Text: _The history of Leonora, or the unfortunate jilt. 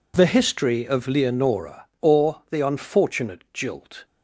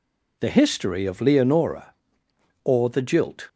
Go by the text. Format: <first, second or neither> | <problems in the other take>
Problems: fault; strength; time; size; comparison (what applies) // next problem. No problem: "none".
first | skips "unfortunate"; at 2.9 s